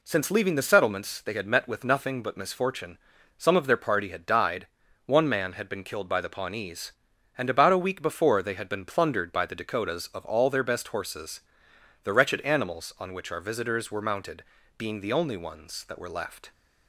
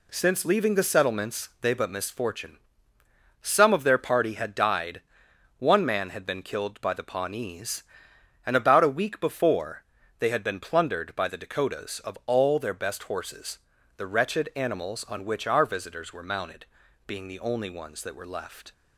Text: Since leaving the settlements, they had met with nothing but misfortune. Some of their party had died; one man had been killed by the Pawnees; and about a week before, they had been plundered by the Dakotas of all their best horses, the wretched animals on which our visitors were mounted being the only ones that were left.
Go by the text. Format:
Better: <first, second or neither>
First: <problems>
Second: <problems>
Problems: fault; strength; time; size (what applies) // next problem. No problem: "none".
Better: first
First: pauses between "mounted" and "being"; slight; at 14.4 s; 0.36 s long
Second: skips "had met with nothing"; at 1.7 s // pauses between "mounted" and "being"; at 16.6 s; 0.42 s long